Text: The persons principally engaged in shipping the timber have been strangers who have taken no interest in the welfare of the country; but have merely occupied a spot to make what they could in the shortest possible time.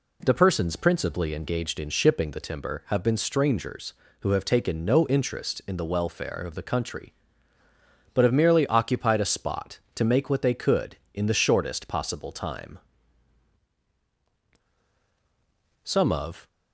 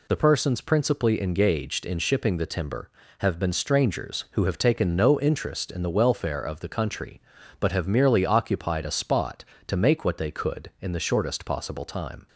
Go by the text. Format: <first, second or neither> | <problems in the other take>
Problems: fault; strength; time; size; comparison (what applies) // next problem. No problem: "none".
second | goes on to say "Some of"; noticeable; from 15.8 s on; 0.64 s long